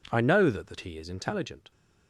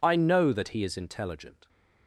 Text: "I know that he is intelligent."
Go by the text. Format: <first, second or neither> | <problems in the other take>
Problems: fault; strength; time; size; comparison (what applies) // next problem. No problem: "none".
second | says "that" twice; at 0.6 s